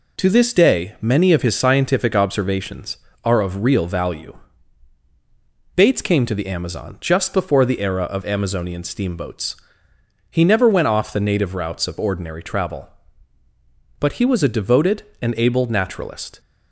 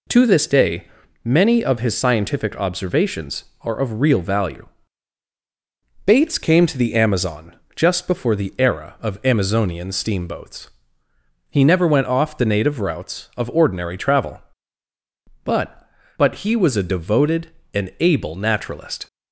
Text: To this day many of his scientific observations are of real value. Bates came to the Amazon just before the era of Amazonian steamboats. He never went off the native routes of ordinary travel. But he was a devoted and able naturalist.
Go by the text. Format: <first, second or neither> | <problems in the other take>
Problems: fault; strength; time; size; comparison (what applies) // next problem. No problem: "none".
first | pauses between "day" and "many"; at 0.8 s; 0.38 s long // pauses between "Amazon" and "just"; slight; at 7.5 s; 0.22 s long // says "But" twice; at 16.1 s